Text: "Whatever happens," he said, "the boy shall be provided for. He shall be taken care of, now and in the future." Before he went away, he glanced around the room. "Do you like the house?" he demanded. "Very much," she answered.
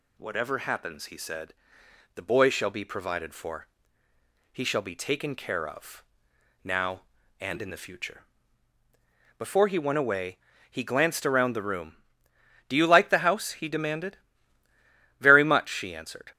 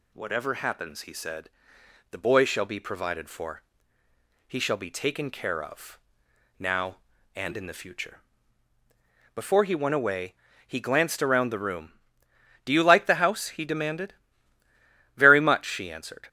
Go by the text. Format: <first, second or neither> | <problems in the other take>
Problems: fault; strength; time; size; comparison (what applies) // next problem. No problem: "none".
neither | none